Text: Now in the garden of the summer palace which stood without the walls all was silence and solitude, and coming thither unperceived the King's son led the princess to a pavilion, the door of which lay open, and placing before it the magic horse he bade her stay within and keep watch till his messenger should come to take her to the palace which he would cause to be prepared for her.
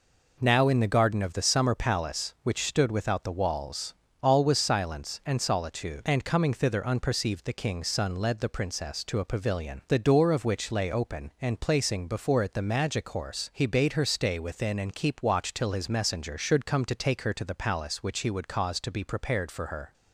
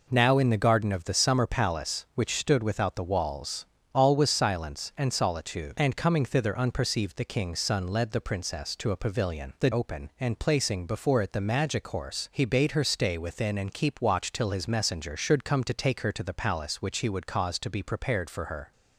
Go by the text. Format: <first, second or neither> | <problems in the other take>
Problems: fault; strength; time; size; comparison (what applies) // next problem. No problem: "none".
first | pauses between "walls" and "all"; slight; at 3.6 s; 0.26 s long; slight in the first // skips "door of which lay"; at 9.7 s